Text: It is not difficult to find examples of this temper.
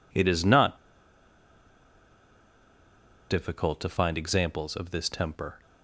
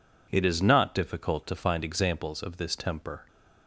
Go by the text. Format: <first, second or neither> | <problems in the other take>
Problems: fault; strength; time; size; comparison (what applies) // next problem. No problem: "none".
second | pauses between "not" and "difficult"; strong; at 0.7 s; 2.5 s long